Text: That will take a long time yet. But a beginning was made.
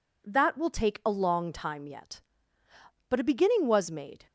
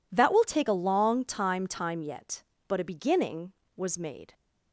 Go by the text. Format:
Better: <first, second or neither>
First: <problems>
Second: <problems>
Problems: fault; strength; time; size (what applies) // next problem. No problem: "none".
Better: first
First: none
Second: says "time" twice; at 1.6 s